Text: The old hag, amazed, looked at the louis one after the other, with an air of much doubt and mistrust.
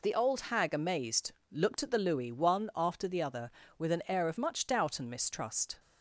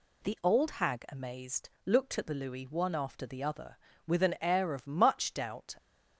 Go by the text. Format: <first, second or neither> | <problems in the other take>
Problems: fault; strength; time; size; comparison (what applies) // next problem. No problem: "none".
first | stops before "and mistrust"; at 5.7 s